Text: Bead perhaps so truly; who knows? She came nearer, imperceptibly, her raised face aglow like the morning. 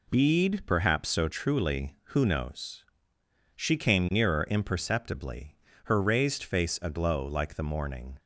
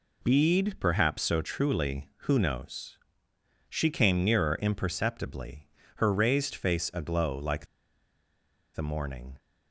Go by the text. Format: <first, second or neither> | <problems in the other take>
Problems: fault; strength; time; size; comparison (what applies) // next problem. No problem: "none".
first | pauses between "like" and "the"; at 7.6 s; 1.0 s long